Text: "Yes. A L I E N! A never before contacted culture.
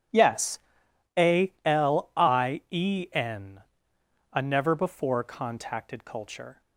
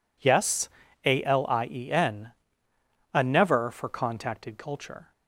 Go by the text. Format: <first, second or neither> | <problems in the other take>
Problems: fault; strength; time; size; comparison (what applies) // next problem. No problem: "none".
first | says "for" for "before"; at 3.6 s